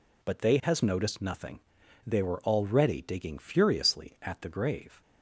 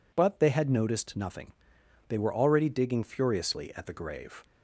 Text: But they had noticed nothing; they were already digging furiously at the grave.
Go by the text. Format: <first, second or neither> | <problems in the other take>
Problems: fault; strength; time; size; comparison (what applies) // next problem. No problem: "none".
second | says "has" for "had"; at 0.6 s